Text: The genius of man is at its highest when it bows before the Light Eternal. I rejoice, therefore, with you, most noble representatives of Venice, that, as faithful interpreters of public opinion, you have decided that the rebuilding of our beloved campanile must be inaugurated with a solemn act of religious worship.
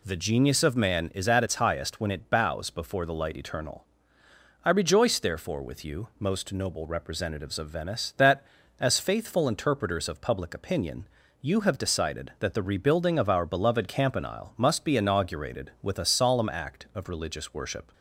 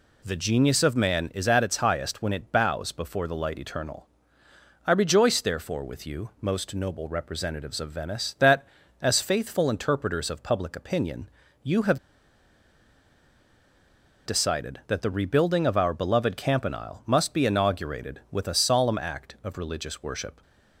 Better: first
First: none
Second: pauses between "have" and "decided"; strong; at 11.9 s; 2.2 s long

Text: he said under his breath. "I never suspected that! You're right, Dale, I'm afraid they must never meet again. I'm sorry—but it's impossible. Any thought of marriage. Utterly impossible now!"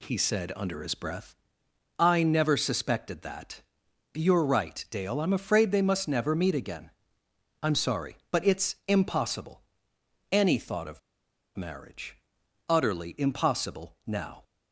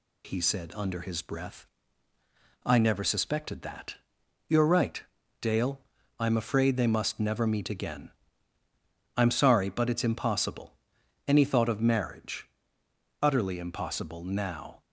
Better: second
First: pauses between "of" and "marriage"; noticeable; at 10.9 s; 0.57 s long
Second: none

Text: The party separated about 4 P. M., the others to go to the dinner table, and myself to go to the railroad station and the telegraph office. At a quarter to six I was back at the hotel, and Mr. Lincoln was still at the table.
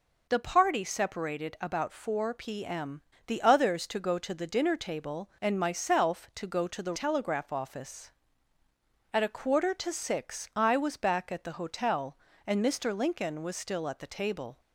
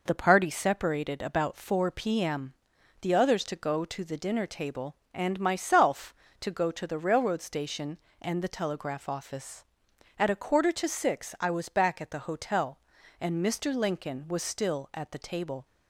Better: second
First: skips "railroad station and the"; at 6.9 s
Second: none

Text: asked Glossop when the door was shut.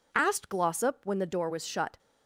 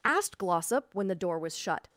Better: neither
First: none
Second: none

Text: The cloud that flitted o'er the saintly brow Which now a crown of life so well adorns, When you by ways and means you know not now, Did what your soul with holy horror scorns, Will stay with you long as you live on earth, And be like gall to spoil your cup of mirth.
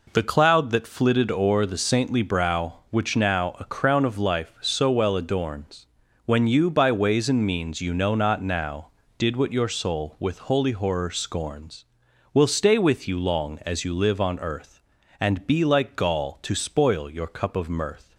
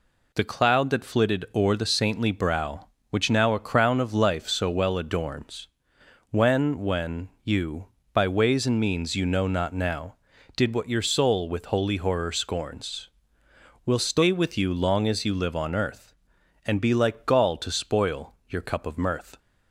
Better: first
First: none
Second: says "When" twice; at 6.8 s // pauses between "spoil" and "your"; slight; at 18.3 s; 0.16 s long

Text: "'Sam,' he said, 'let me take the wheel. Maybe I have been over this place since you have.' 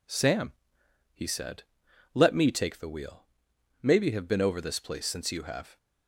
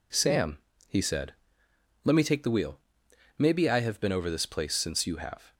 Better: second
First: skips "I"; at 4.1 s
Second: none

